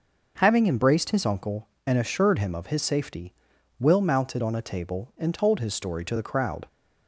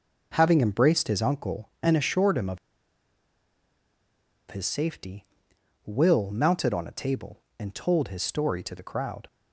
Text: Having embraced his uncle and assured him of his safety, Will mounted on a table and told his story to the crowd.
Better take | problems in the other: first | pauses between "of" and "his"; strong; at 2.5 s; 1.9 s long

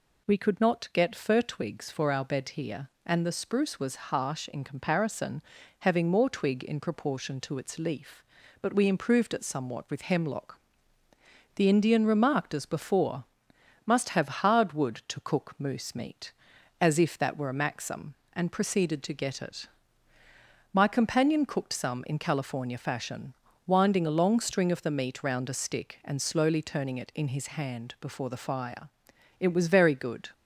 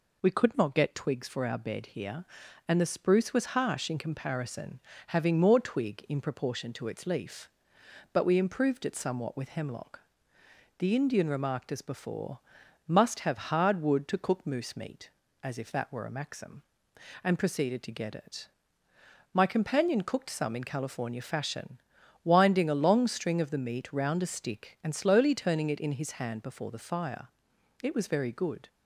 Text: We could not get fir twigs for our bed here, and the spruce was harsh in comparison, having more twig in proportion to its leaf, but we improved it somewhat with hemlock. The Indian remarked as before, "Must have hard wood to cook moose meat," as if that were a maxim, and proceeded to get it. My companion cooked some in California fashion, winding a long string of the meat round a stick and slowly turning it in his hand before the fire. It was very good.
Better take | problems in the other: first | skips "fir"; at 0.9 s

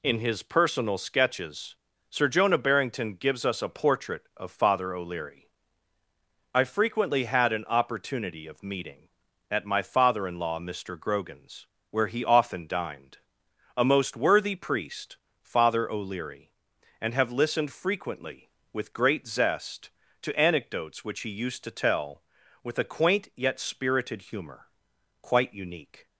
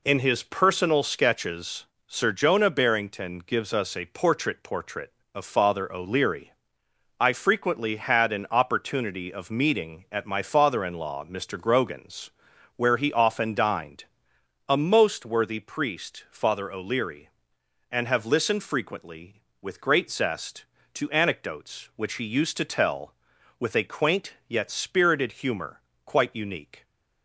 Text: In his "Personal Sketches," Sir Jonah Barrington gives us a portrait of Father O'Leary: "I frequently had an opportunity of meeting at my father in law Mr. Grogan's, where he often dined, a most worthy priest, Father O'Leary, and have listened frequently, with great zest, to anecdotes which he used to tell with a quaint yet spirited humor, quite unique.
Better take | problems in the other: first | says "portrait" twice; at 4.6 s

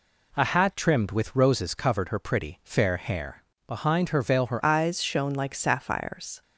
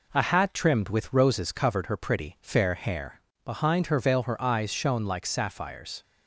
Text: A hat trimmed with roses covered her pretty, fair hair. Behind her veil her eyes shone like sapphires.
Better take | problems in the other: second | changes voice at "eyes"; from 4.6 s on; 1.8 s long

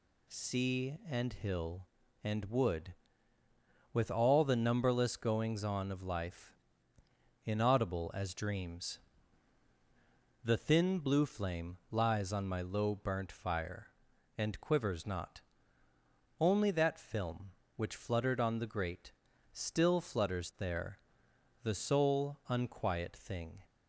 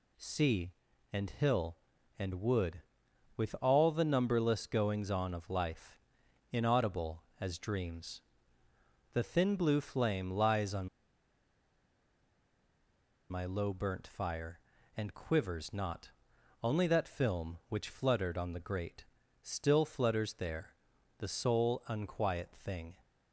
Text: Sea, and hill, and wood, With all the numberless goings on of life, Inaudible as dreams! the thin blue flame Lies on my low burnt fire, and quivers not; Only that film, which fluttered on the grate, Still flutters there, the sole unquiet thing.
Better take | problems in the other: first | pauses between "on" and "my"; strong; at 10.8 s; 2.4 s long

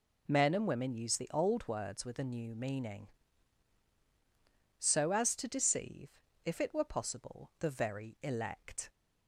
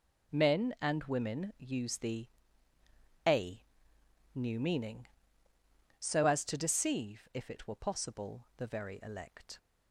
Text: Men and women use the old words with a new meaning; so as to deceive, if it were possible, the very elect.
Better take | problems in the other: first | skips "old words with"; at 2.7 s // pauses between "a" and "new"; noticeable; at 3.6 s; 0.72 s long

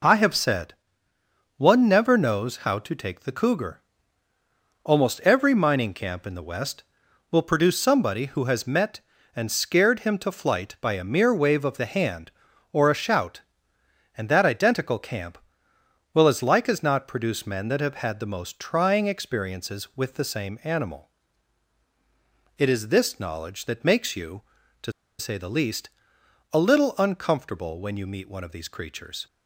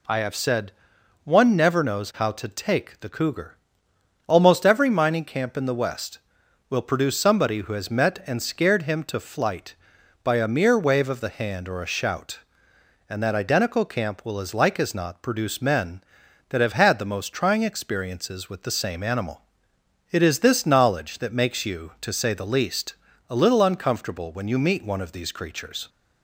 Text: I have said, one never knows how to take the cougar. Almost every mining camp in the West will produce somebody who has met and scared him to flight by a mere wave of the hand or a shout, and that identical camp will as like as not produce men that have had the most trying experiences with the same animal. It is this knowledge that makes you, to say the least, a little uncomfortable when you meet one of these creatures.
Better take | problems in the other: second | pauses between "to" and "say"; slight; at 24.9 s; 0.27 s long

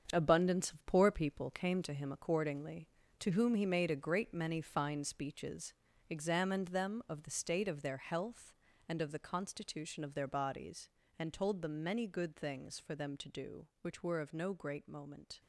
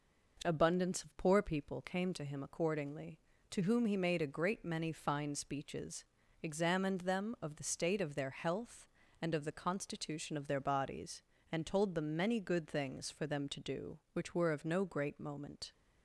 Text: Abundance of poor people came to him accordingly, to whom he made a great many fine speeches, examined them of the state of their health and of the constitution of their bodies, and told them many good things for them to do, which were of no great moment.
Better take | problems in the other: second | gets quieter; strong; throughout; 8.5 dB

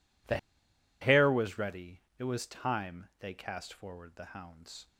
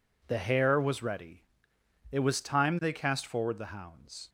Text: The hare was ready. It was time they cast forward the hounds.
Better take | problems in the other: second | pauses between "The" and "hare"; noticeable; at 0.3 s; 0.63 s long

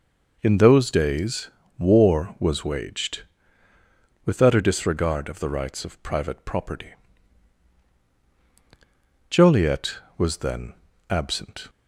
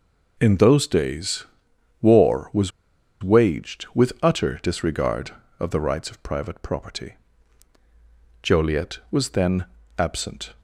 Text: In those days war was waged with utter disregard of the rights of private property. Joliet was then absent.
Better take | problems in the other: first | pauses between "days" and "war"; noticeable; at 1.4 s; 0.56 s long; slight in the first // pauses between "was" and "waged"; noticeable; at 2.7 s; 0.51 s long // pauses between "then" and "absent"; slight; at 9.6 s; 0.32 s long; slight in the first

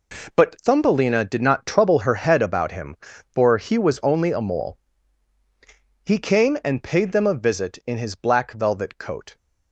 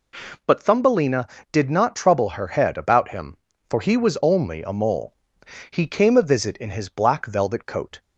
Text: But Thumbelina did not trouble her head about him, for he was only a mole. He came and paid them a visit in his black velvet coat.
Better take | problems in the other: first | skips "and paid them"; at 6.1 s

